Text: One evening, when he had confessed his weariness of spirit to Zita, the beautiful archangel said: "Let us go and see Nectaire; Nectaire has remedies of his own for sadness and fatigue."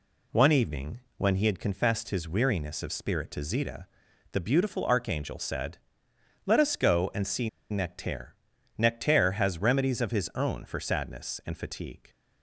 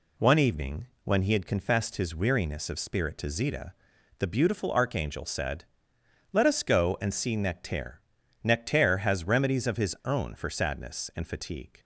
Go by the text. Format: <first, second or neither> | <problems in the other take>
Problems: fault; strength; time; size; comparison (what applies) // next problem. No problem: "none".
second | pauses between "see" and "Nectaire"; slight; at 7.4 s; 0.21 s long